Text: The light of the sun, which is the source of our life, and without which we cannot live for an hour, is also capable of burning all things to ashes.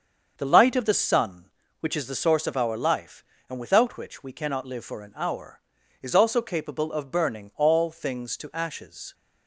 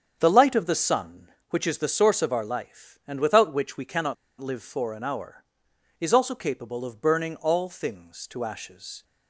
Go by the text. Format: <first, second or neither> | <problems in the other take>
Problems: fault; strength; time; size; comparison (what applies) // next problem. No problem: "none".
first | starts louder than the rest; strong; until 1.2 s; 7.5 dB; also in the first // pauses between "cannot" and "live"; slight; at 4.1 s; 0.26 s long